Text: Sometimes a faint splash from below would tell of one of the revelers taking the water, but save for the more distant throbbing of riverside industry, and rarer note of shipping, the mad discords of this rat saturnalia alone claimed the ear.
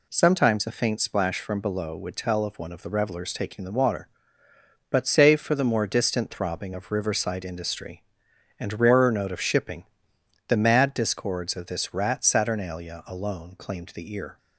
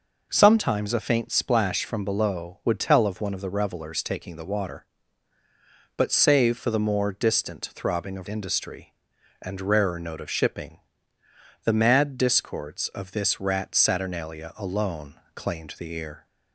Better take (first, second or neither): first